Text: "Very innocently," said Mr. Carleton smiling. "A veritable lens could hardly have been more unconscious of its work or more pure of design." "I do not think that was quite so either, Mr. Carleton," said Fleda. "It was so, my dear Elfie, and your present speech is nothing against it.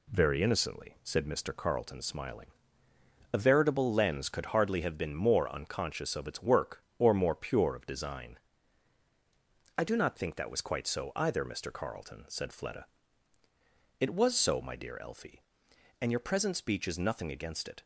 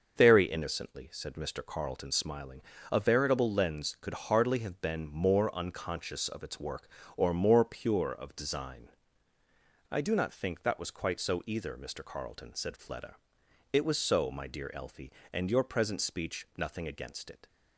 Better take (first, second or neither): first